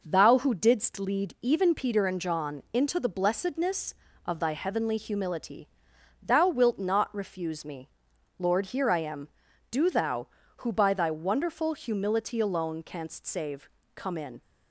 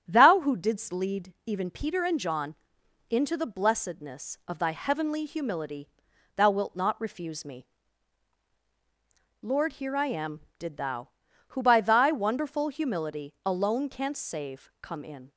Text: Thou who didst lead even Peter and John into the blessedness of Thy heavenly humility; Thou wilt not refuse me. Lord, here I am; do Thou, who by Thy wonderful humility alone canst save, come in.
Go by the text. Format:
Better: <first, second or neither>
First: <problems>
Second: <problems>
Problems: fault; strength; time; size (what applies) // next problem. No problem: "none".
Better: first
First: none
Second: starts louder than the rest; strong; until 1.0 s; 8.5 dB // pauses between "John" and "into"; noticeable; at 2.5 s; 0.56 s long // says "did" for "do"; at 10.5 s